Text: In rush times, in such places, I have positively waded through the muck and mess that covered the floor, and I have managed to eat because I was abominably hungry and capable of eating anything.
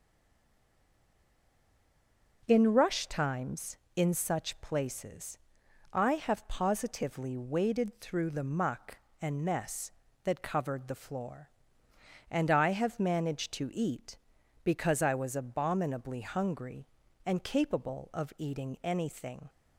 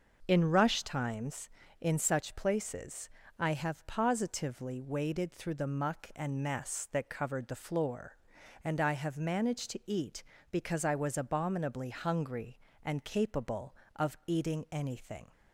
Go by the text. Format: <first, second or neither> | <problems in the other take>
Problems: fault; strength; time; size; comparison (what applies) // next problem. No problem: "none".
second | stays silent before the first word; until 2.4 s; 2.4 s long